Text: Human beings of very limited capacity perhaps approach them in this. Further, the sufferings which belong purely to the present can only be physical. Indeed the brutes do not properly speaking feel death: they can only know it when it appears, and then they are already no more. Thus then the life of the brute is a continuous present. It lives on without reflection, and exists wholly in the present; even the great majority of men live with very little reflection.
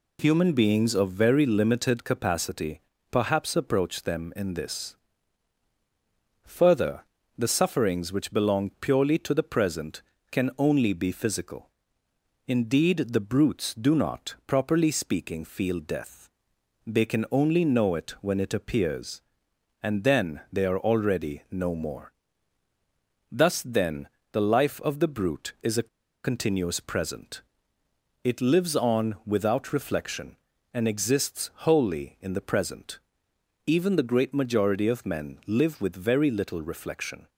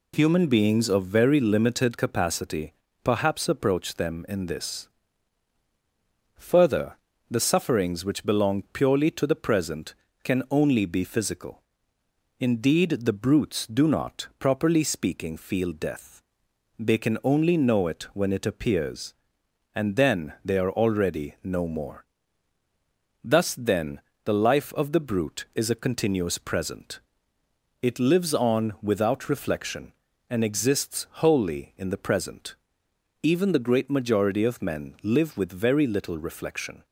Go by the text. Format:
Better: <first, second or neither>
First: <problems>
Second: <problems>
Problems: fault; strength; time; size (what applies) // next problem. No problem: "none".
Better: second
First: pauses between "capacity" and "perhaps"; slight; at 2.8 s; 0.28 s long // pauses between "then" and "the"; slight; at 24.0 s; 0.26 s long // pauses between "a" and "continuous"; slight; at 25.8 s; 0.35 s long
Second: pauses between "capacity" and "perhaps"; slight; at 2.7 s; 0.28 s long // pauses between "then" and "the"; slight; at 23.9 s; 0.26 s long